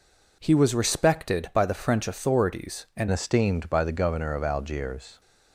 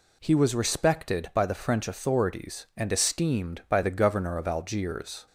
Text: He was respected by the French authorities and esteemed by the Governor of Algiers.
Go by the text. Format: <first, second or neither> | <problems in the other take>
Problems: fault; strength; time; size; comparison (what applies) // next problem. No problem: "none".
second | changes voice at "esteemed"; from 3.1 s on; 2.0 s long